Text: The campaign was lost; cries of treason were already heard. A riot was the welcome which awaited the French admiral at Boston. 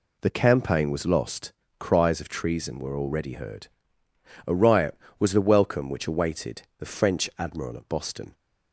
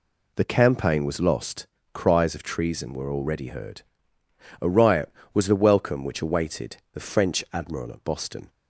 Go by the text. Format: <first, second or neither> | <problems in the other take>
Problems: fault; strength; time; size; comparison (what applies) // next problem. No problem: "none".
neither | pauses between "awaited" and "the"; slight; the same in both